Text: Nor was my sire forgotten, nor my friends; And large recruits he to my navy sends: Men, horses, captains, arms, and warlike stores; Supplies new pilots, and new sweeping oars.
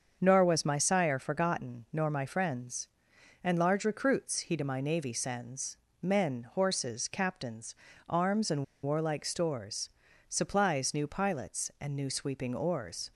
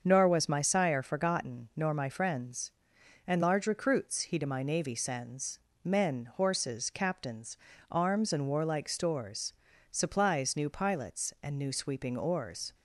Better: second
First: starts louder than the rest; until 1.2 s; 6.5 dB // pauses between "and" and "warlike"; slight; at 8.6 s; 0.19 s long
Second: starts louder than the rest; until 1.0 s; 6.5 dB

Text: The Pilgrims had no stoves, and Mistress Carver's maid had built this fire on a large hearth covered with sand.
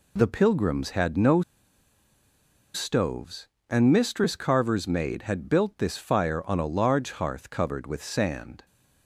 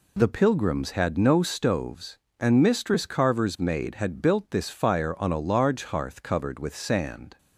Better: second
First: pauses between "no" and "stoves"; strong; at 1.4 s; 1.3 s long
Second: none

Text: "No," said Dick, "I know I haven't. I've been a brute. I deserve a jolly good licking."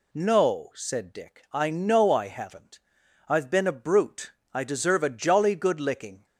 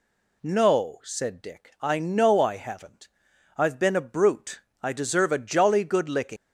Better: first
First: none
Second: leaves "licking" unfinished; at 6.3 s; 175 ms

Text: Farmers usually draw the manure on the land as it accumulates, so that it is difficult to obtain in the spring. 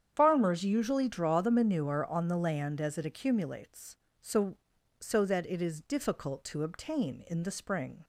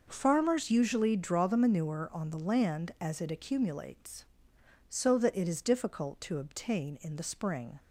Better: second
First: starts louder than the rest; strong; until 1.1 s; 8.5 dB // says "so" twice; at 5.0 s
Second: none

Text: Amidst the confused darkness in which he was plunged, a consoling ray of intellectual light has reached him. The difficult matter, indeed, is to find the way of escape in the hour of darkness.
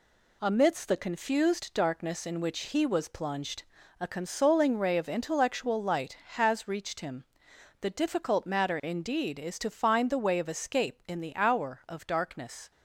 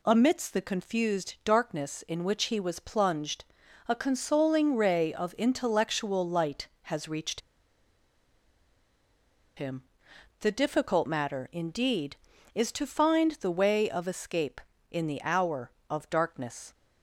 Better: first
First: none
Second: pauses between "reached" and "him"; strong; at 7.4 s; 2.1 s long

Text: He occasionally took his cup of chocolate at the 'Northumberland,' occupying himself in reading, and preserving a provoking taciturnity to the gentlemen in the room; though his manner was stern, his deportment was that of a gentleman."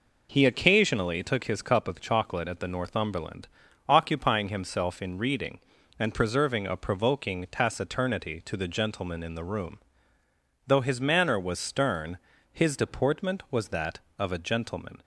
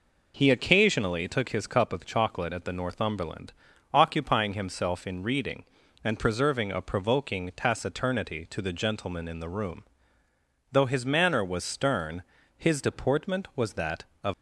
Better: first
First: none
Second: stops before "a gentleman"; at 14.3 s

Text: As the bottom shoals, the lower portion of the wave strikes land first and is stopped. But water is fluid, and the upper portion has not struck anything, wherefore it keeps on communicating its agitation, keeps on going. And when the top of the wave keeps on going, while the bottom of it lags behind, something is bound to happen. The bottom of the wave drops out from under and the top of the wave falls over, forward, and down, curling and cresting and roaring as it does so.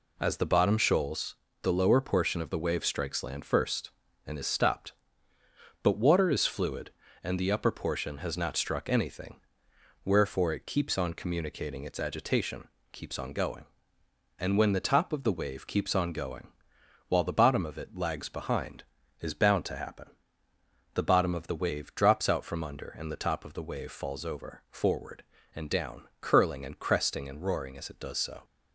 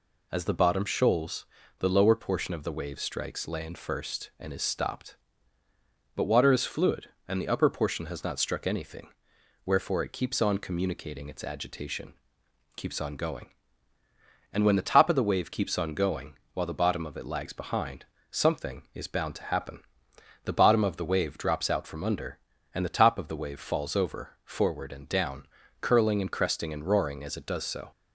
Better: second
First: skips "something"; at 19.0 s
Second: none

